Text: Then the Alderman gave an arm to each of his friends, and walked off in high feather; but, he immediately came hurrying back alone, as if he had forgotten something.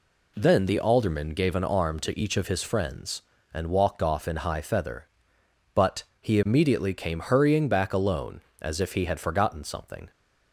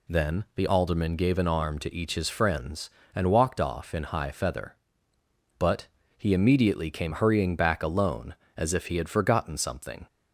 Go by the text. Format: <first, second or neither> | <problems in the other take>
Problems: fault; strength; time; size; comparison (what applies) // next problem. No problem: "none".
first | skips "of"; at 2.1 s